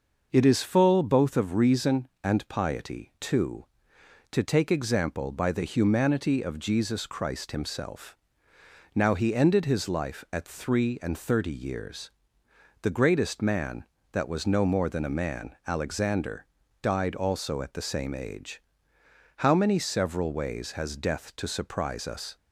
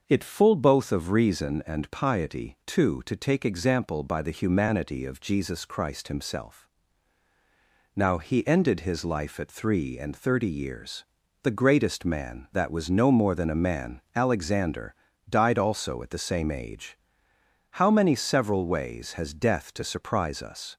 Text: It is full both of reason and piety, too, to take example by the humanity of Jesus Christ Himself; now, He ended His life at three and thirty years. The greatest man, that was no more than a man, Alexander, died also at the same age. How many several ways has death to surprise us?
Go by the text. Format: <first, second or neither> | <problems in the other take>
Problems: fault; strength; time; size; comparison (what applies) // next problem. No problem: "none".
first | starts louder than the rest; until 1.0 s; 6.5 dB // skips "is"; at 0.2 s